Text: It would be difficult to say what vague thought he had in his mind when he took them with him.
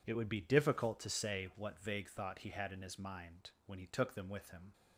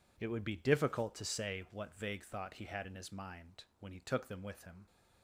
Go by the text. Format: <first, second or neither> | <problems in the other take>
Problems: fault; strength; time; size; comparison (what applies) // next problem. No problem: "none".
neither | pauses between "mind" and "when"; slight; the same in both